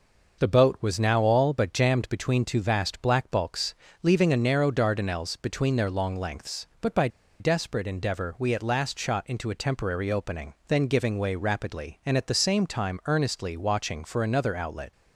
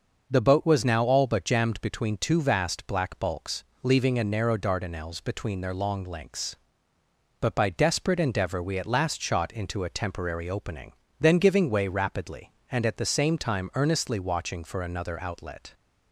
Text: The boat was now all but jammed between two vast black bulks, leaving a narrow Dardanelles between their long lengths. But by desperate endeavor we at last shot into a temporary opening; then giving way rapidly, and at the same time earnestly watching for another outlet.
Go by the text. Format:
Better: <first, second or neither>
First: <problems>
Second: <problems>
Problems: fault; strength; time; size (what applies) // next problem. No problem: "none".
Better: second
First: pauses between "by" and "desperate"; slight; at 7.0 s; 0.31 s long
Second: none